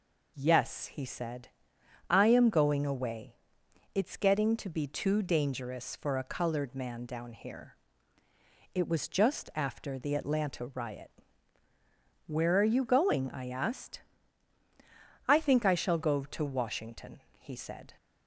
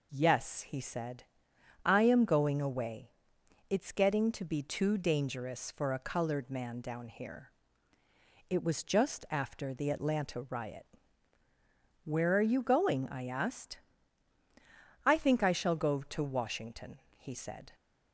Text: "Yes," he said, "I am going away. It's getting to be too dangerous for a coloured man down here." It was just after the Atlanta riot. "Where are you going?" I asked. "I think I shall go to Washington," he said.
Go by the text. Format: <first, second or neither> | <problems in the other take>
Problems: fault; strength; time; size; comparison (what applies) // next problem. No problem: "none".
neither | none